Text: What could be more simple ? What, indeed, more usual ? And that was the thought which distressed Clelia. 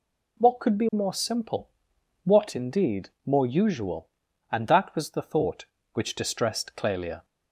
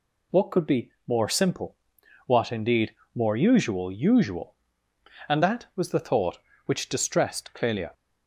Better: first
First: none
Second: pauses between "be" and "more"; slight; at 0.9 s; 0.18 s long // says "usual" twice; at 3.9 s

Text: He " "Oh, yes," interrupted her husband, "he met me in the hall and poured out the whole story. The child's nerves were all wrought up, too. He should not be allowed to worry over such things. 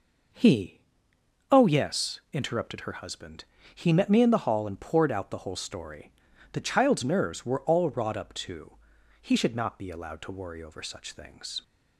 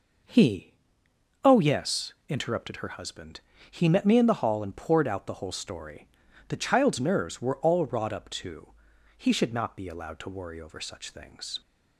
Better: neither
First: none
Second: none

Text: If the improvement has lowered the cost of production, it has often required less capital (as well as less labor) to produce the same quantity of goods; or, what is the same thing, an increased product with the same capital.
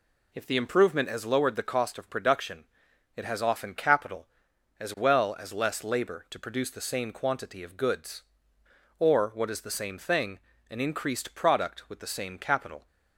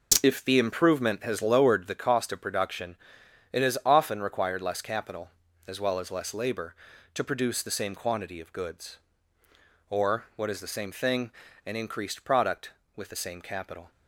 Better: second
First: skips "required less"; at 3.7 s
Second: none

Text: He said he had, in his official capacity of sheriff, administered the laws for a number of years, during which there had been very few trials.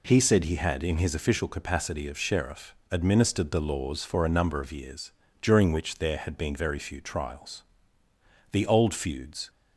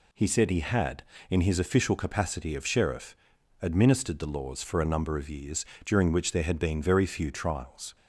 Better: second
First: goes on to say "The old feuds"; noticeable; from 8.5 s on; 0.98 s long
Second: none

